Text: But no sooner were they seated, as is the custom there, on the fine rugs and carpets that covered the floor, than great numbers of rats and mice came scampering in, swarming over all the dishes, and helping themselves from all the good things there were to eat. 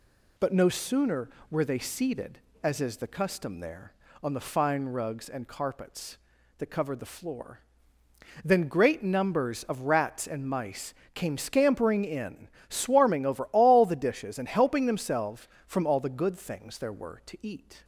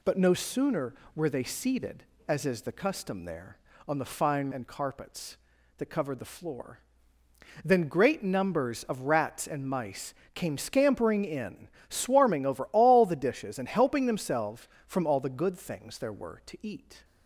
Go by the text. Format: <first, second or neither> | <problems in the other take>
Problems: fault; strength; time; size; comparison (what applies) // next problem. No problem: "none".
first | skips "rugs"; at 4.5 s // pauses between "mice" and "came"; slight; at 10.1 s; 0.22 s long; slight in the first